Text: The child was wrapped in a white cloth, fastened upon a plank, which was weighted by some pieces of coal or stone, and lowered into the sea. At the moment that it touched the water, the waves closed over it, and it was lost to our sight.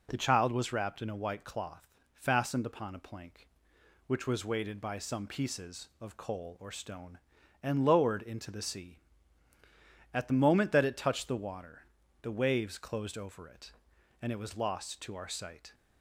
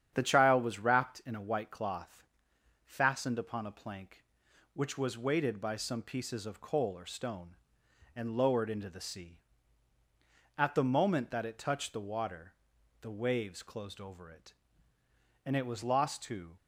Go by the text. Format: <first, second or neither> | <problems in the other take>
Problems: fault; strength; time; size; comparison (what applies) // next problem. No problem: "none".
first | starts louder than the rest; strong; until 1.1 s; 9 dB // stops before "our sight"; at 16.5 s